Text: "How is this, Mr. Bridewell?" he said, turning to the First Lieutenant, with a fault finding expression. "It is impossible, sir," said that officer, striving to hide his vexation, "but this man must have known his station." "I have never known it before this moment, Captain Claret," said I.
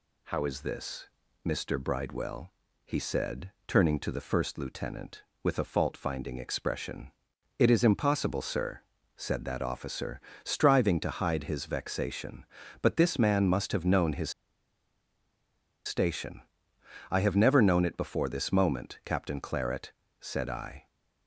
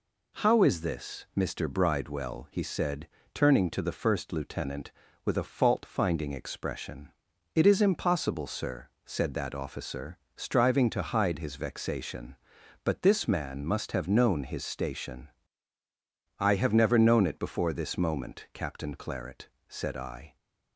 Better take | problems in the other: second | pauses between "his" and "station"; strong; at 14.2 s; 1.5 s long

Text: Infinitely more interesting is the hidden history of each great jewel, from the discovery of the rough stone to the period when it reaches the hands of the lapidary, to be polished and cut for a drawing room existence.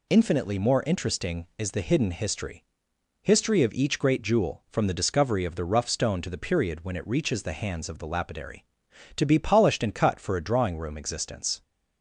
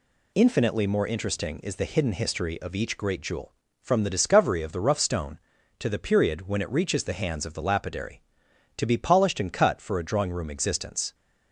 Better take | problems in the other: second | says "history" twice; at 3.2 s

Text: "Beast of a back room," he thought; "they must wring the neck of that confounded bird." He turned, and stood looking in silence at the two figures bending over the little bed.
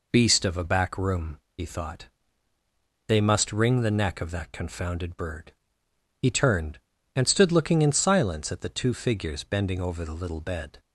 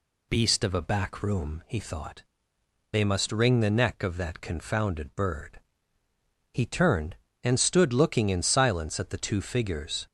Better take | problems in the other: first | stops before "bending over the little bed"; at 10.0 s

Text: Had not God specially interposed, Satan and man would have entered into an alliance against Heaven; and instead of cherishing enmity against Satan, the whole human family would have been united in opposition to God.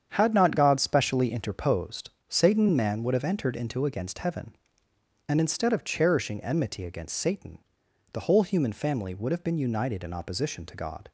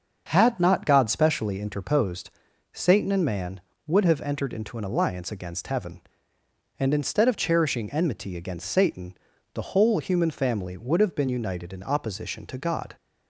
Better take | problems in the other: second | starts louder than the rest; strong; until 1.1 s; 8 dB; also in the second // skips "an alliance"; at 3.8 s

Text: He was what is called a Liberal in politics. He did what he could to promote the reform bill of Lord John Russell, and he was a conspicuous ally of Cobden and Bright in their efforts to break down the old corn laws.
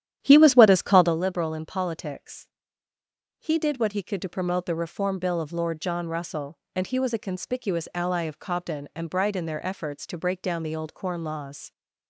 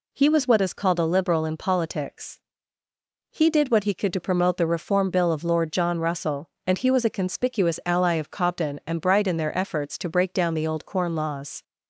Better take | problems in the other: second | starts louder than the rest; strong; until 1.2 s; 10.5 dB

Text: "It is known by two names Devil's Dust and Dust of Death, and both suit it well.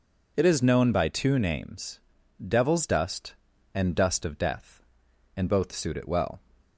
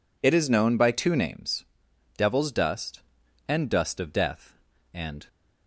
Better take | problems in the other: first | pauses between "names" and "Devil's"; noticeable; at 1.6 s; 0.52 s long; noticeable in the first // stops before "both suit it well"; at 5.2 s

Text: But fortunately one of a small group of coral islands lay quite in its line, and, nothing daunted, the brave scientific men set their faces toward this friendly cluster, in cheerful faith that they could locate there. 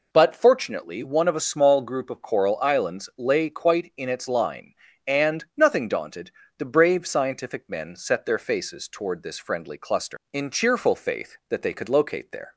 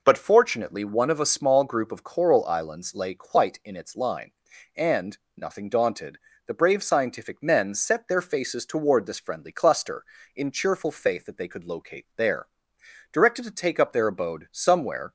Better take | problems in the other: first | goes on to say "Directed to take up their abode somewhere"; strong; from 13.1 s on; 2.0 s long

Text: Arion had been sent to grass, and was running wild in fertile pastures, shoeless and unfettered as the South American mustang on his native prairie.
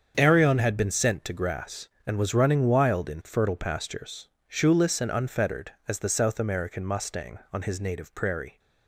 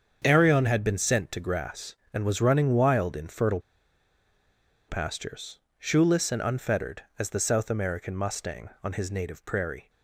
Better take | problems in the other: first | starts louder than the rest; until 1.2 s; 7 dB; strong in the first // pauses between "fertile" and "pastures"; strong; at 3.5 s; 1.2 s long

